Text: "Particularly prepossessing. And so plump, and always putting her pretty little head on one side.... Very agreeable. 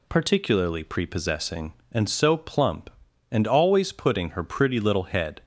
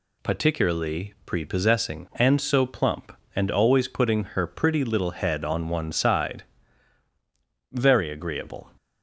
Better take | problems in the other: second | stops before "on one side Very agreeable"; at 5.4 s

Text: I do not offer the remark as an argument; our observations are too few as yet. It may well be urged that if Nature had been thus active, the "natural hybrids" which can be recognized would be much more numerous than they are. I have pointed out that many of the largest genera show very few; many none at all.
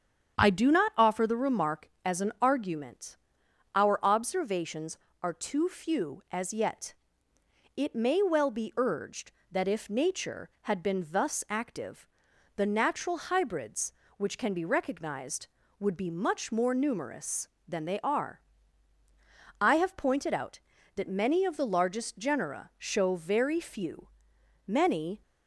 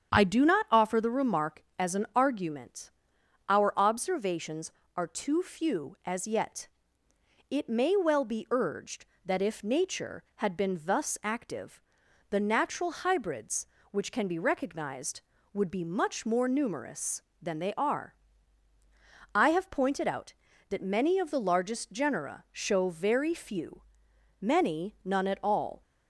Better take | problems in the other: second | starts louder than the rest; strong; until 1.4 s; 8 dB; strong in the second // stops before "none at all"; at 25.2 s

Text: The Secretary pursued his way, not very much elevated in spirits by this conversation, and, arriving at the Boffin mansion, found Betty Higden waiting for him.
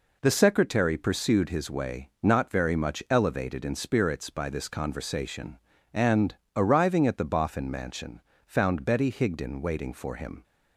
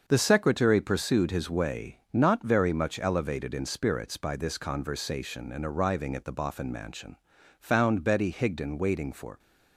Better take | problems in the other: first | starts louder than the rest; until 1.0 s; 6.5 dB // stops before "him"; at 9.3 s

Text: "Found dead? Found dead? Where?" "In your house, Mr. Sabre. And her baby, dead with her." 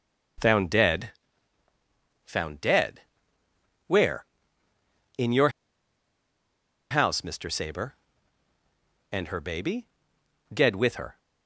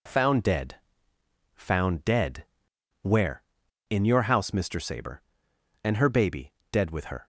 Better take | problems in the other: second | pauses between "your" and "house"; strong; at 5.4 s; 1.4 s long

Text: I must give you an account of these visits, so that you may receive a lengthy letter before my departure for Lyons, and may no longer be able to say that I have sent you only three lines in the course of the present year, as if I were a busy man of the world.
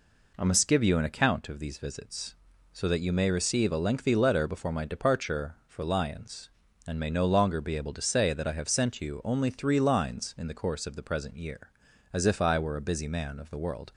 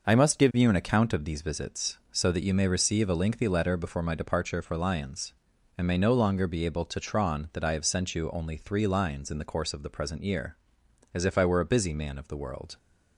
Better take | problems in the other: first | says "tron" for "say"; at 7.0 s

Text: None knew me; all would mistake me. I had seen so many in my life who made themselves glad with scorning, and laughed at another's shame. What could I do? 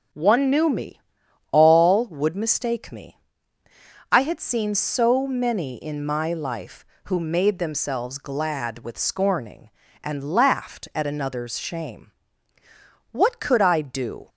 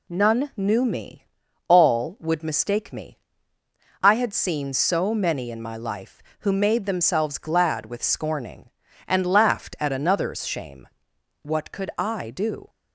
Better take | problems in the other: second | starts louder than the rest; until 1.6 s; 6 dB // says "One" for "None"; at 0.1 s

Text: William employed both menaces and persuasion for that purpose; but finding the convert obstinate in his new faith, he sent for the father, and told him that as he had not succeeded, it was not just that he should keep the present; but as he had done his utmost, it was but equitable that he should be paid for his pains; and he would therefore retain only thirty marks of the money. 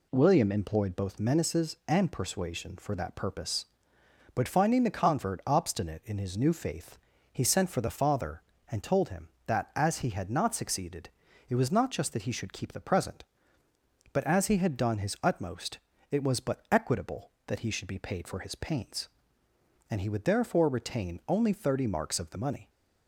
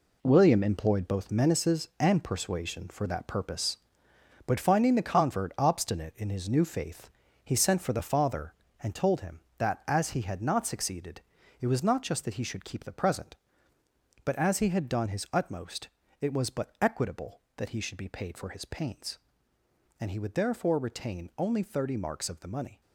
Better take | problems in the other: first | gets quieter; strong; throughout; 9 dB

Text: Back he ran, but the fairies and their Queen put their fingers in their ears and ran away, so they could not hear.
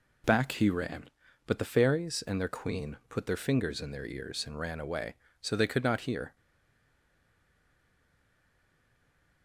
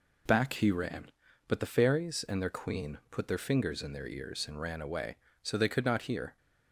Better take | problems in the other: second | stays silent after the last word; strong; from 6.3 s on; 3.1 s long

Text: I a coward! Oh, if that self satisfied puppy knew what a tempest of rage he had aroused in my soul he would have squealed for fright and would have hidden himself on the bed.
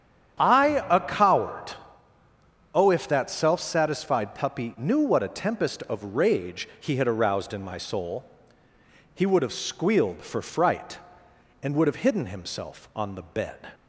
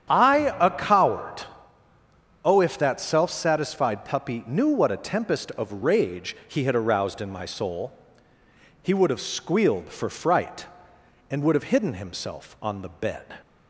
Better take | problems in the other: neither | starts louder than the rest; strong; the same in both // pauses between "soul" and "he"; noticeable; the same in both

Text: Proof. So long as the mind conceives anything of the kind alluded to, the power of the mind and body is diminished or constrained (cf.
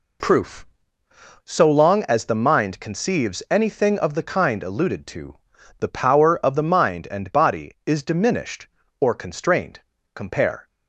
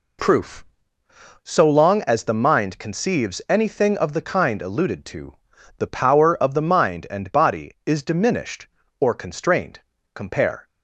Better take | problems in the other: neither | none

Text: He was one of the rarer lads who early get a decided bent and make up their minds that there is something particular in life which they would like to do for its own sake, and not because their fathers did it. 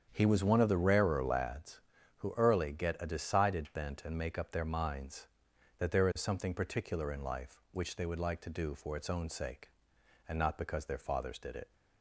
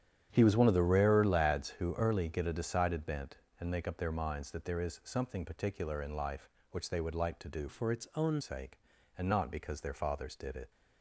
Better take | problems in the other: first | starts louder than the rest; strong; until 1.3 s; 9.5 dB; strong in the first // changes voice from "for" to "own"; from 7.6 to 8.3 s; 0.7 s long

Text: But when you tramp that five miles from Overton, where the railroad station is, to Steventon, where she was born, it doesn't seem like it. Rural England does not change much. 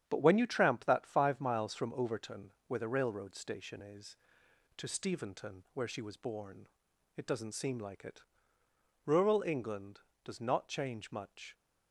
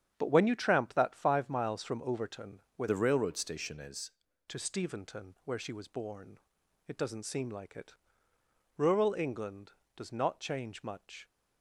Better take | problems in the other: first | starts louder than the rest; strong; until 1.1 s; 8.5 dB; strong in the first // changes voice from "the" to "is"; from 2.8 to 4.1 s; 1.3 s long

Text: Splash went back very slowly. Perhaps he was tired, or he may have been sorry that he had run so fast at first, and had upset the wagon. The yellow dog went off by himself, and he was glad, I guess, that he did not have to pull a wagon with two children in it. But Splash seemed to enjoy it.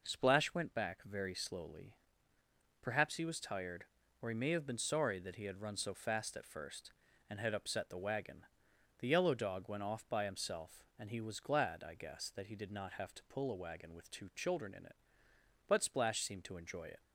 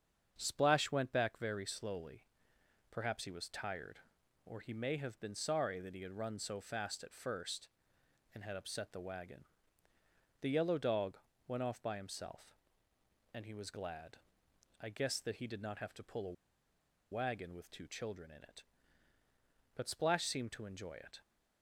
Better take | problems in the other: first | starts louder than the rest; strong; until 1.3 s; 7.5 dB // pauses between "dog" and "went"; slight; at 11.1 s; 0.30 s long // pauses between "a" and "wagon"; noticeable; at 16.3 s; 0.78 s long

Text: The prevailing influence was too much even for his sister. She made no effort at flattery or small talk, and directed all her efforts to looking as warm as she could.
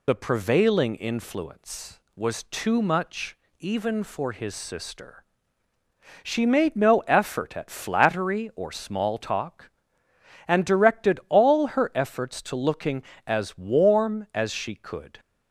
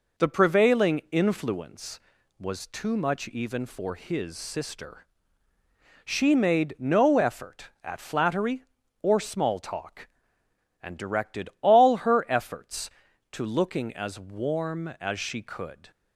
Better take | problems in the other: second | loses the start of "The"; at 0.0 s; 65 ms // pauses between "much" and "even"; slight; at 3.3 s; 0.24 s long

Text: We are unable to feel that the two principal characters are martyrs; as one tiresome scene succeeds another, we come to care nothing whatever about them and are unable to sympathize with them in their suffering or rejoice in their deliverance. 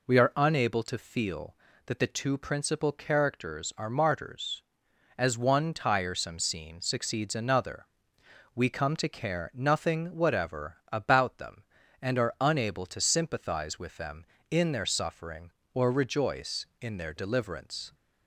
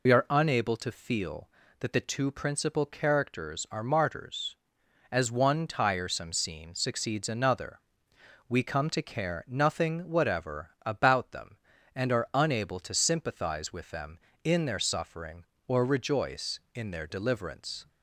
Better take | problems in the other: first | loses the start of "We"; at 0.0 s; 55 ms // pauses between "whatever" and "about"; slight; at 10.6 s; 0.16 s long; slight in the first

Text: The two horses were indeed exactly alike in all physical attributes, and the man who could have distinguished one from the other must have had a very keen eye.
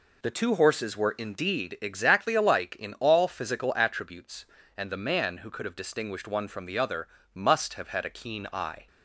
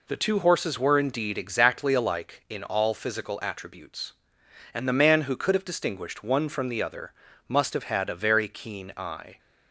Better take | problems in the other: second | pauses between "other" and "must"; slight; at 7.0 s; 0.26 s long; slight in the second // skips "very"; at 8.1 s

